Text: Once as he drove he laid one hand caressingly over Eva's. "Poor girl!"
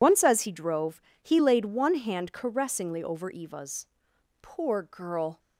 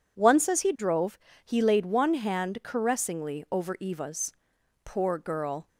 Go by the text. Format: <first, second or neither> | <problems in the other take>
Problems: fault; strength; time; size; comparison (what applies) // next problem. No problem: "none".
second | loses the start of "Once"; at 0.0 s; 55 ms // pauses between "drove" and "he"; slight; at 1.0 s; 0.22 s long; slight in the second